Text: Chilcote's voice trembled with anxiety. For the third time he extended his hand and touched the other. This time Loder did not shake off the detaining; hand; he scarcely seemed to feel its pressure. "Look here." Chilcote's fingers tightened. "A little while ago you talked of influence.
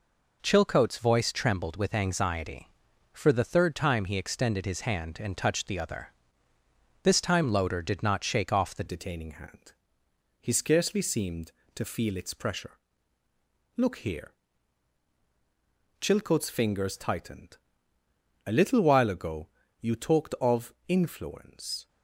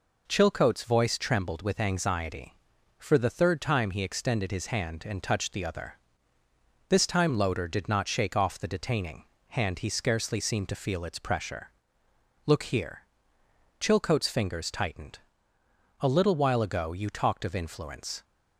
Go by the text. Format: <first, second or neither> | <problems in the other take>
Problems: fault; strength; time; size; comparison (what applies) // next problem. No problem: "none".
second | changes voice at "detaining"; from 8.8 s on; 13.0 s long // pauses between "ago" and "you"; slight; at 19.4 s; 0.34 s long // pauses between "of" and "influence"; slight; at 20.7 s; 0.16 s long